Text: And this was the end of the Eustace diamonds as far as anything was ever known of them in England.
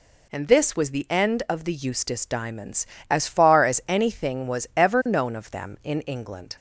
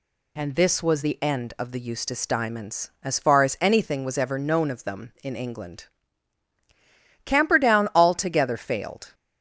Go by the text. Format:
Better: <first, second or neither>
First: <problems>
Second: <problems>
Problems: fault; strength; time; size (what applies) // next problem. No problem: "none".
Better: first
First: none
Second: goes on to say "Camperdown altogether failed"; strong; from 7.2 s on; 1.8 s long